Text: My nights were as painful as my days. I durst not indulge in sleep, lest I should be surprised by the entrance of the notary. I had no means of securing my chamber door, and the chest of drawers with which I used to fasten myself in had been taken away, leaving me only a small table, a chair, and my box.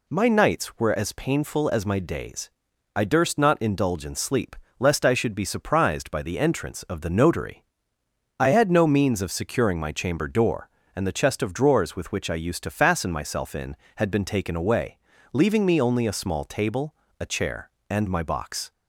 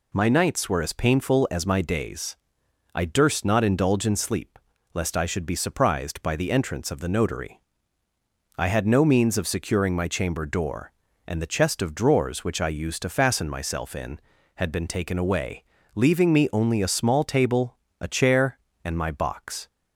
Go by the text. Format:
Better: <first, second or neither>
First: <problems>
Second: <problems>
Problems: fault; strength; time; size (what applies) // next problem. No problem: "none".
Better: first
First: none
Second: skips "with"; at 12.4 s